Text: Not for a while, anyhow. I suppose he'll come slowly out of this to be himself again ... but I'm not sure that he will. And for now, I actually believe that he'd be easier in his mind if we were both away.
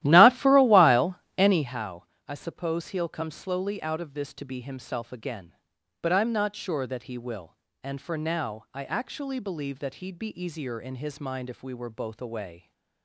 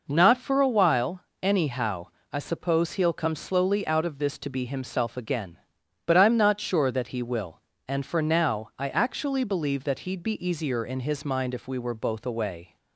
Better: second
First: starts louder than the rest; strong; until 1.8 s; 14.5 dB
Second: none

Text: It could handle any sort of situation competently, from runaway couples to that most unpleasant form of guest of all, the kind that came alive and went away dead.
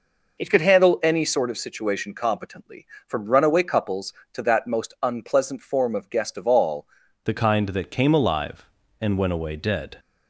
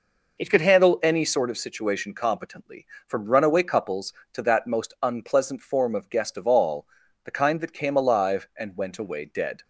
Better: second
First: changes voice at "the"; from 7.2 s on; 2.7 s long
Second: none

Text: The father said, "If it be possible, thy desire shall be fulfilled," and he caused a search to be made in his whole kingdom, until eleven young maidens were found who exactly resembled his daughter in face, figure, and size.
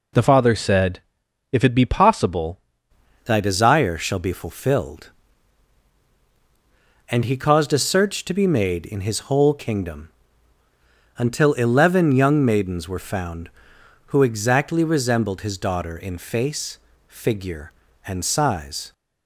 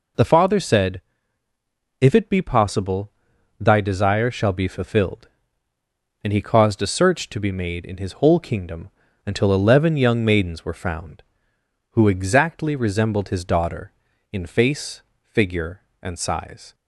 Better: second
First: changes voice at "thy"; from 3.2 s on; 15.7 s long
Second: none

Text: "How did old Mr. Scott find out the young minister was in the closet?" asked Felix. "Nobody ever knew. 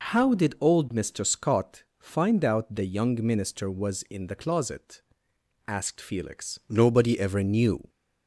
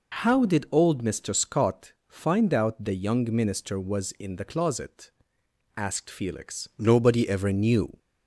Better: neither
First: none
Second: none

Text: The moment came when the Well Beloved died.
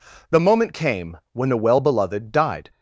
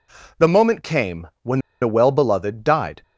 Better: first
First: pauses between "came" and "when"; slight; at 1.1 s; 0.16 s long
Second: pauses between "came" and "when"; slight; at 1.2 s; 0.16 s long // pauses between "when" and "the"; slight; at 1.5 s; 0.22 s long

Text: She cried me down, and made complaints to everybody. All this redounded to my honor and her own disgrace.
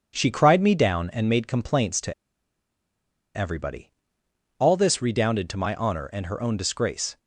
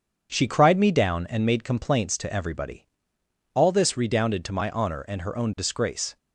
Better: second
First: starts louder than the rest; strong; until 1.1 s; 7 dB // pauses between "to" and "everybody"; at 2.1 s; 1.2 s long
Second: starts louder than the rest; until 1.3 s; 7 dB

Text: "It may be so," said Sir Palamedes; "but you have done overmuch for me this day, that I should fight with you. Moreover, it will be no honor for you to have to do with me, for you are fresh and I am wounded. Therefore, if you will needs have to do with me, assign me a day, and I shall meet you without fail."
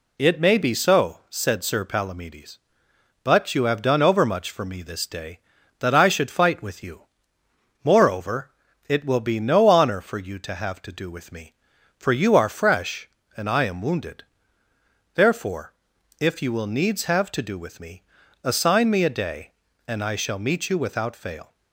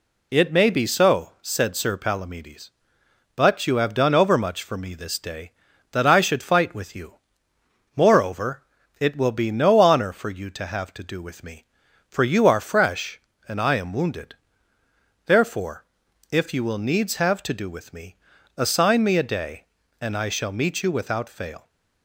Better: neither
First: none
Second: none

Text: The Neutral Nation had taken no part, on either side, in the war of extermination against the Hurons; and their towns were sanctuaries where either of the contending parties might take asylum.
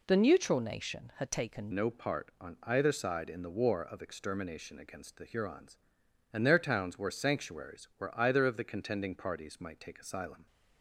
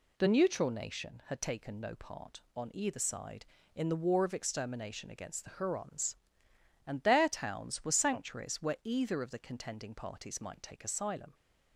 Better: second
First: changes voice at "no"; from 1.7 s on; 8.7 s long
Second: none

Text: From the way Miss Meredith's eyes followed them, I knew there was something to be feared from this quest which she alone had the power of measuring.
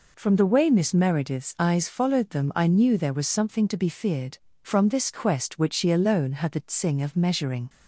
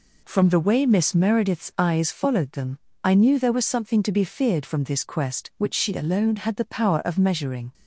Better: second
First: says "tsing" for "power"; at 6.5 s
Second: none

